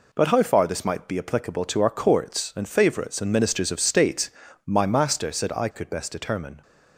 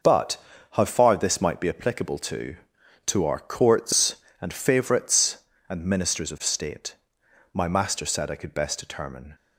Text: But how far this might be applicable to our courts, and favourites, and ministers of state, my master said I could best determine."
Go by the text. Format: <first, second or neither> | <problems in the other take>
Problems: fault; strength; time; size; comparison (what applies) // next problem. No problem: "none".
first | pauses between "But" and "how"; slight; at 0.3 s; 0.34 s long // says "to" twice; at 3.0 s